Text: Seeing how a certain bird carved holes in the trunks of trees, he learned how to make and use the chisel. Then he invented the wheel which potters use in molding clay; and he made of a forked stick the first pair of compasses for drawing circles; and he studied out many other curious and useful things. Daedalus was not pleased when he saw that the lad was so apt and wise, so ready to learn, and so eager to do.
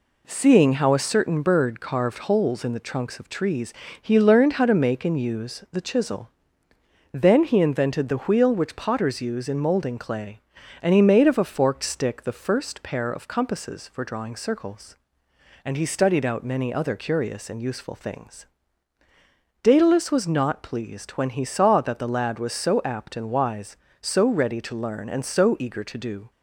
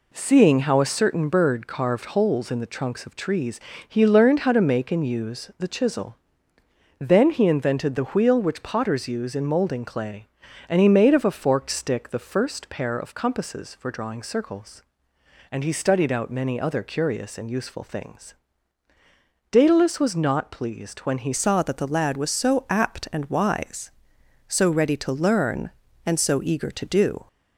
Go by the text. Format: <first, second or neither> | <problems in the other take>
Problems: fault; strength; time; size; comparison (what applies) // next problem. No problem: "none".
first | changes voice at "saw"; from 21.3 s on; 5.9 s long